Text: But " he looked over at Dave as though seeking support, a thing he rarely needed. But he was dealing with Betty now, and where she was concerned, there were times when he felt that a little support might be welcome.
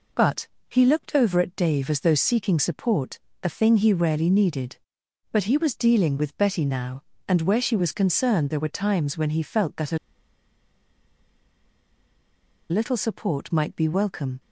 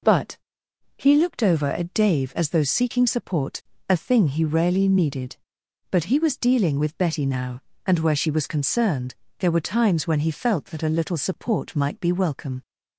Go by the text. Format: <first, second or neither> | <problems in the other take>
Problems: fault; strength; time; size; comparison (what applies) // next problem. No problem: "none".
second | pauses between "a" and "little"; strong; at 9.9 s; 2.7 s long